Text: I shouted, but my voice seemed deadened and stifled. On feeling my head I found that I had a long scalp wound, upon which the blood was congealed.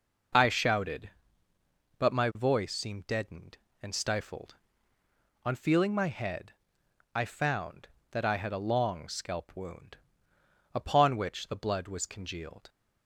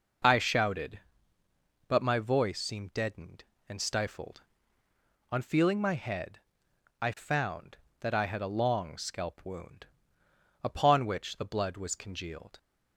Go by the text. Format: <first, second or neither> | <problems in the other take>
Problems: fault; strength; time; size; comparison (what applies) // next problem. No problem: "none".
neither | pauses between "head" and "I"; noticeable; the same in both